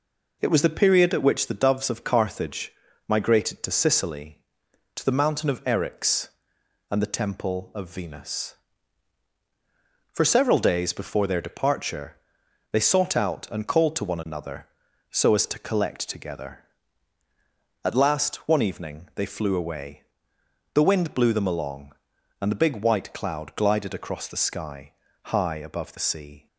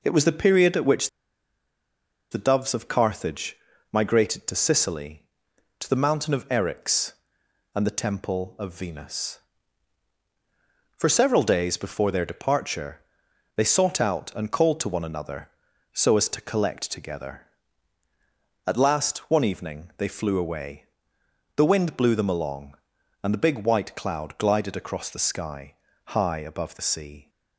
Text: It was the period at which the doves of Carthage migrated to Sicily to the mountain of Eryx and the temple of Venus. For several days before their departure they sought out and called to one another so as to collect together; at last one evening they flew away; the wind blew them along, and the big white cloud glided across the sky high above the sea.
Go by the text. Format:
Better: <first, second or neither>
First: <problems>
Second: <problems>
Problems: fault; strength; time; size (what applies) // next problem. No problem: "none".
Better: first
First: pauses between "Carthage" and "migrated"; at 2.7 s; 0.38 s long // pauses between "departure" and "they"; noticeable; at 12.1 s; 0.54 s long // pauses between "sky" and "high"; slight; at 24.9 s; 0.32 s long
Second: pauses between "which" and "the"; at 1.0 s; 1.2 s long // pauses between "Carthage" and "migrated"; at 3.5 s; 0.38 s long // pauses between "departure" and "they"; noticeable; at 13.0 s; 0.54 s long // pauses between "sky" and "high"; slight; at 25.7 s; 0.32 s long